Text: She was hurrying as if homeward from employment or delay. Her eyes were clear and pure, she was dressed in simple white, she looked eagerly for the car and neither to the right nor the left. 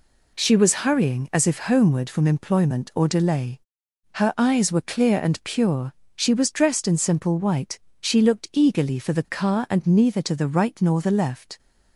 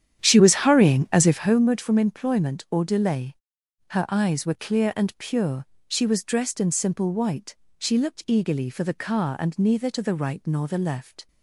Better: first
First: none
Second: starts louder than the rest; strong; until 1.6 s; 9.5 dB

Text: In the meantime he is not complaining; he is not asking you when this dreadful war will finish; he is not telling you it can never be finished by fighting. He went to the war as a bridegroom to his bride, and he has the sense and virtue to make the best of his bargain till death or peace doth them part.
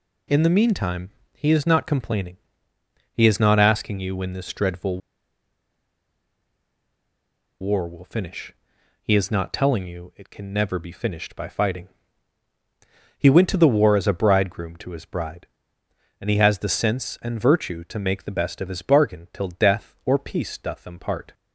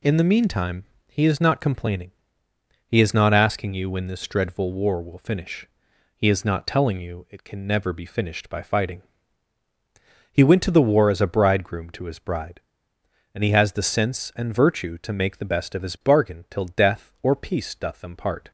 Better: second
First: pauses between "meantime" and "he"; slight; at 1.0 s; 0.24 s long // pauses between "dreadful" and "war"; strong; at 4.9 s; 2.6 s long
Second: pauses between "meantime" and "he"; slight; at 0.8 s; 0.24 s long

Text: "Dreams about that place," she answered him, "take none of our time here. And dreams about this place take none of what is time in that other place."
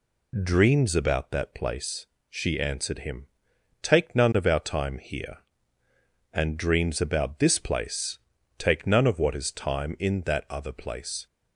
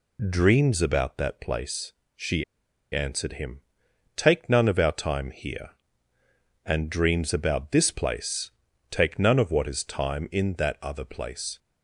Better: first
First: pauses between "place" and "take"; at 8.1 s; 0.40 s long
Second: pauses between "she" and "answered"; noticeable; at 2.4 s; 0.48 s long // pauses between "place" and "take"; at 8.5 s; 0.40 s long

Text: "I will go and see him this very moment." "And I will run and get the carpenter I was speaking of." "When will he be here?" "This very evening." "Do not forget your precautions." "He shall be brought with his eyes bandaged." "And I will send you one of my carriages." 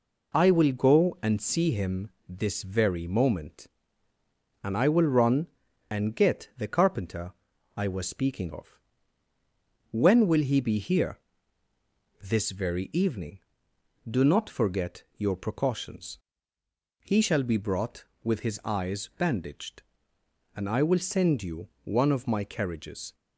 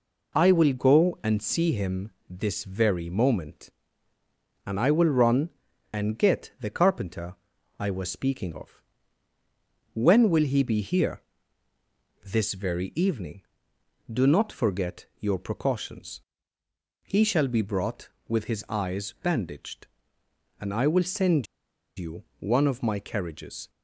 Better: first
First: pauses between "him" and "this"; slight; at 2.0 s; 0.18 s long // pauses between "carpenter" and "I"; at 7.3 s; 0.44 s long // pauses between "you" and "one"; slight; at 21.6 s; 0.16 s long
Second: pauses between "him" and "this"; slight; at 2.1 s; 0.18 s long // pauses between "carpenter" and "I"; at 7.3 s; 0.44 s long // pauses between "send" and "you"; noticeable; at 21.4 s; 0.51 s long // pauses between "you" and "one"; slight; at 22.2 s; 0.16 s long

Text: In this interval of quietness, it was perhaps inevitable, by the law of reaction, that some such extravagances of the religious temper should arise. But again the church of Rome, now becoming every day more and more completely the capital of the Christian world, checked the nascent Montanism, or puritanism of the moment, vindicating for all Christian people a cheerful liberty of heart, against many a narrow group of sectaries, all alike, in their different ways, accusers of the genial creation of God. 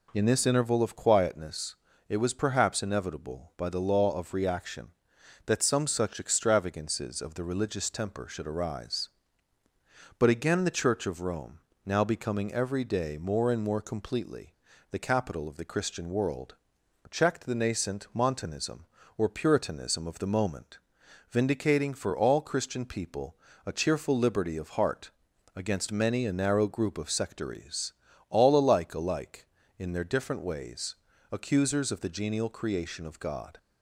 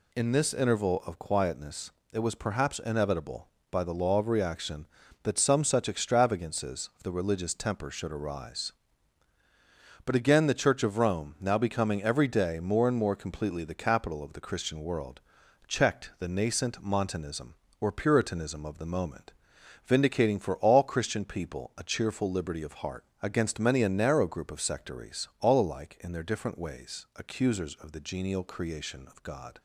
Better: second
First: pauses between "completely" and "the"; at 14.5 s; 0.38 s long // pauses between "people" and "a"; slight; at 23.3 s; 0.30 s long // says "alike" twice; at 28.9 s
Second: none

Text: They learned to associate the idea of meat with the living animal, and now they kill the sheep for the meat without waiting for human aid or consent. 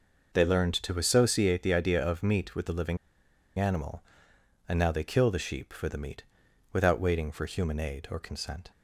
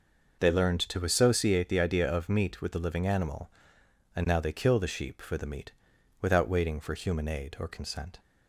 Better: second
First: pauses between "living" and "animal"; noticeable; at 2.9 s; 0.61 s long // pauses between "meat" and "without"; noticeable; at 6.2 s; 0.50 s long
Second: pauses between "meat" and "without"; noticeable; at 5.7 s; 0.50 s long

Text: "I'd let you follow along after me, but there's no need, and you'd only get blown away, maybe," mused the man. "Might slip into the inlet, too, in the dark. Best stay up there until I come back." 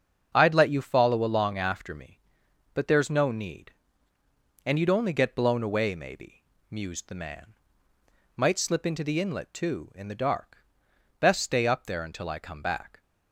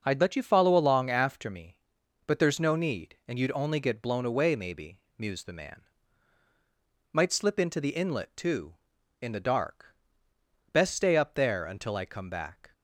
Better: neither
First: starts louder than the rest; strong; until 1.3 s; 7.5 dB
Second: starts louder than the rest; until 1.0 s; 6 dB

